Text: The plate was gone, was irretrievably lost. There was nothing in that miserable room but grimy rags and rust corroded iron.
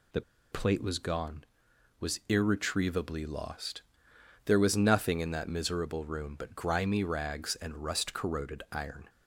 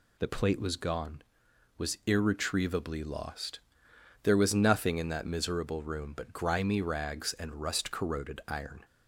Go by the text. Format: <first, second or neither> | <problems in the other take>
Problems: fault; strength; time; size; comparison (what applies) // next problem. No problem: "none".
second | pauses between "The" and "plate"; slight; at 0.2 s; 0.30 s long